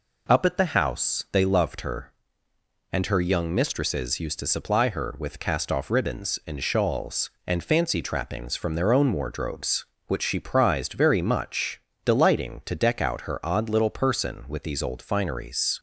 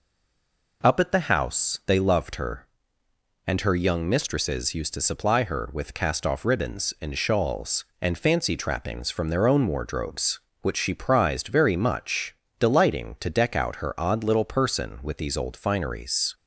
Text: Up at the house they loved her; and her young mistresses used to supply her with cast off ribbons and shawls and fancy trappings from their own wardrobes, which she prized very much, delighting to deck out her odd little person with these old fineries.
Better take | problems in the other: first | stays silent before the first word; slight; until 0.8 s; 0.8 s long

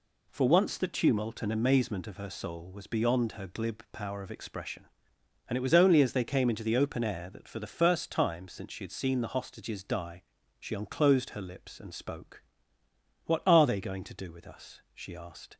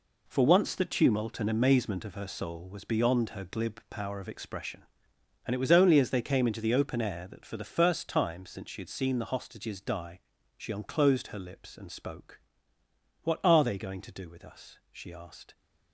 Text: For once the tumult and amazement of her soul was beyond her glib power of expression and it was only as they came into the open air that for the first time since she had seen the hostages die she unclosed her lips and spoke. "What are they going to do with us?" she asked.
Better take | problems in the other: first | gets quieter; strong; throughout; 10.5 dB // pauses between "die" and "she"; at 10.1 s; 0.38 s long; also in the first

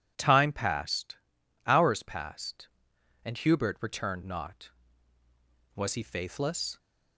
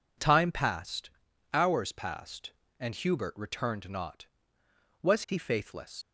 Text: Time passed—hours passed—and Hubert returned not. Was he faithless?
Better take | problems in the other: first | leaves "faithless" unfinished; at 6.0 s; 70 ms

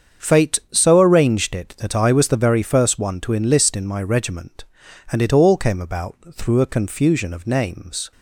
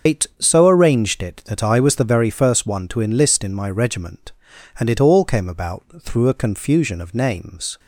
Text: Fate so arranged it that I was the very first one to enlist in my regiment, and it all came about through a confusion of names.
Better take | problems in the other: first | loses the start of "Fate"; at 0.0 s; 165 ms // starts louder than the rest; until 1.1 s; 7 dB; strong in the first

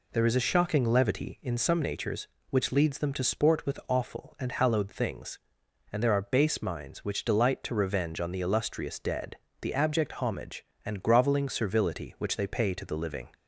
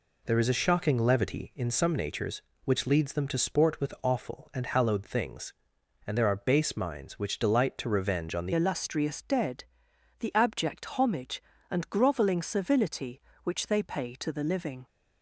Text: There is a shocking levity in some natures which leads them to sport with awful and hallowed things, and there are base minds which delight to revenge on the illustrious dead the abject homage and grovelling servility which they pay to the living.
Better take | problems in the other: first | changes voice at "illustrious"; from 8.5 s on; 6.3 s long // pauses between "dead" and "the"; noticeable; at 9.6 s; 0.56 s long; slight in the first

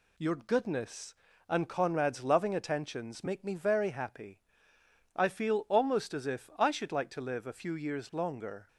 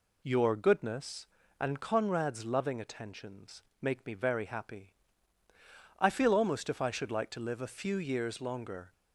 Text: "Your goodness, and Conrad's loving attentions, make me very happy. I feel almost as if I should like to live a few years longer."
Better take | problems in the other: first | skips "as"; at 6.6 s

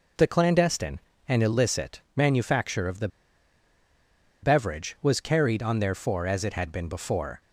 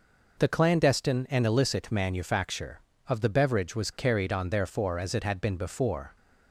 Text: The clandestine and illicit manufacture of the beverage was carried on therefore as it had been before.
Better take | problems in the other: second | pauses between "illicit" and "manufacture"; slight; at 1.9 s; 0.16 s long // pauses between "the" and "beverage"; strong; at 3.0 s; 1.3 s long

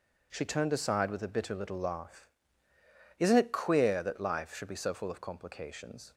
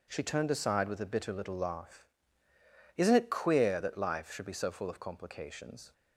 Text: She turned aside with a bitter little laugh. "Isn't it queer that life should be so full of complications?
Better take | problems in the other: neither | none

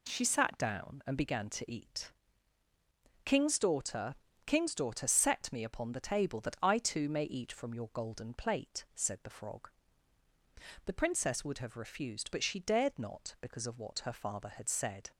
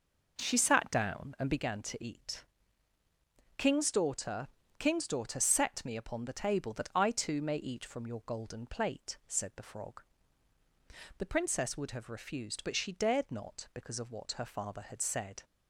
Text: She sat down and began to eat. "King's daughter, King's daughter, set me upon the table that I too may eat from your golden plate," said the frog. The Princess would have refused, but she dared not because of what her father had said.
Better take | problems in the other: first | starts louder than the rest; noticeable; until 1.7 s; 5.5 dB

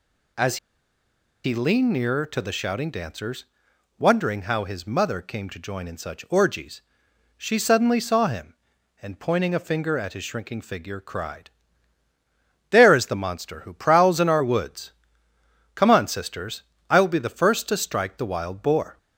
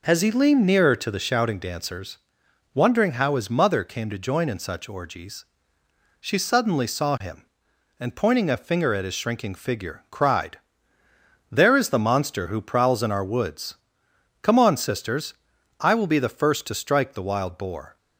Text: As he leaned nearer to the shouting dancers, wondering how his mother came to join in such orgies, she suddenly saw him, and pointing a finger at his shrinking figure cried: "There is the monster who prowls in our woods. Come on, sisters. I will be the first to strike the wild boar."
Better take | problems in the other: second | pauses between "As" and "he"; noticeable; at 0.5 s; 0.88 s long

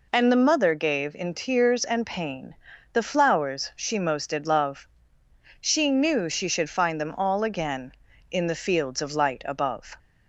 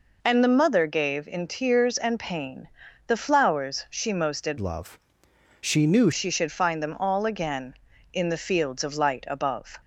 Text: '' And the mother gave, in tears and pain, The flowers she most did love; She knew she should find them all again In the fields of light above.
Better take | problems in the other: first | changes voice from "love" to "knew"; from 4.5 to 6.0 s; 1.5 s long

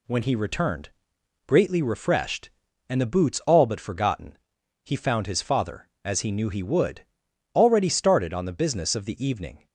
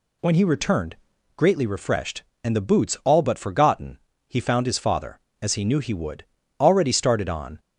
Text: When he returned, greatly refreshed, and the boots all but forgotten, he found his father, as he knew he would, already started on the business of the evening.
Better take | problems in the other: first | stops before "the business of the evening"; at 7.5 s

